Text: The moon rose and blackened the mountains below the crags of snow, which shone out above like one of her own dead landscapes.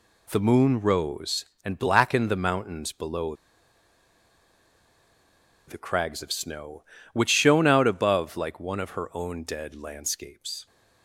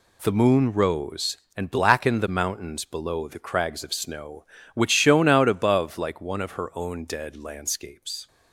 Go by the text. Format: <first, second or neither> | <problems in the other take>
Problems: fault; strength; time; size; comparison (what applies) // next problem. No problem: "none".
second | pauses between "below" and "the"; strong; at 3.3 s; 2.3 s long